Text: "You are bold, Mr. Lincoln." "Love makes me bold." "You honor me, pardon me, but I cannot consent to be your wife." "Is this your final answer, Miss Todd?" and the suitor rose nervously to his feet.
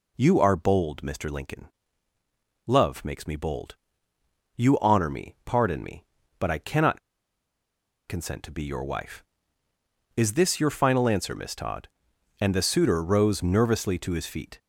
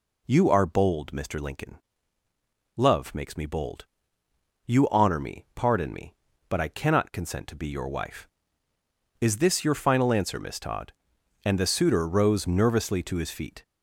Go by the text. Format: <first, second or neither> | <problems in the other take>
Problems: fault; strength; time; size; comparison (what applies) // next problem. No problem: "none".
second | pauses between "cannot" and "consent"; at 6.9 s; 1.0 s long